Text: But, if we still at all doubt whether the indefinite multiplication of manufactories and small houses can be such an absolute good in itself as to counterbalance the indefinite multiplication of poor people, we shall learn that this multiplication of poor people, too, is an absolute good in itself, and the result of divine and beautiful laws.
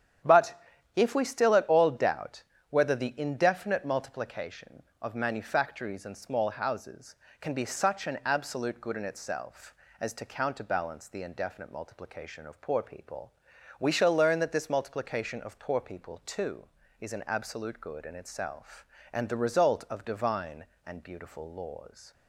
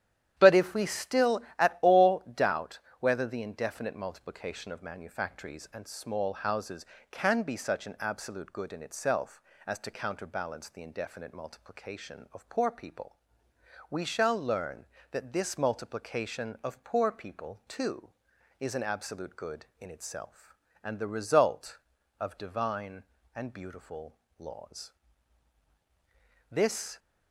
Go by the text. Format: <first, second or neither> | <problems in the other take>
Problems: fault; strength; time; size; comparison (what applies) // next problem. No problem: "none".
first | starts louder than the rest; strong; until 1.3 s; 10.5 dB; strong in the first // pauses between "doubt" and "whether"; slight; at 2.7 s; 0.20 s long; slight in the first // pauses between "beautiful" and "laws"; slight; at 24.1 s; 0.22 s long // goes on to say "This"; slight; from 26.5 s on; 0.48 s long